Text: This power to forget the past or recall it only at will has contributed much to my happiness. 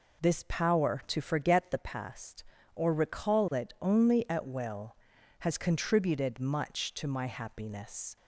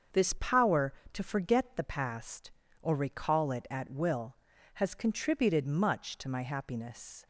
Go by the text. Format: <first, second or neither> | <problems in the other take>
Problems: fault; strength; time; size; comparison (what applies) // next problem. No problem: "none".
first | starts louder than the rest; until 1.3 s; 7 dB // skips "only"; at 3.6 s